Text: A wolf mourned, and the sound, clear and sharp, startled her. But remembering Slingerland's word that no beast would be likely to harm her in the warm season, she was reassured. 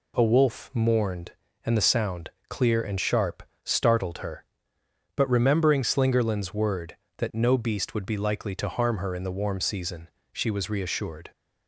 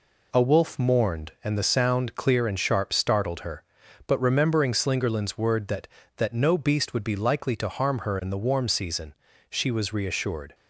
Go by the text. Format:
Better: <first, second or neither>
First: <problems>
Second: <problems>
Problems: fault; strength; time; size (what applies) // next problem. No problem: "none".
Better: first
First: none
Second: says "that" twice; at 6.1 s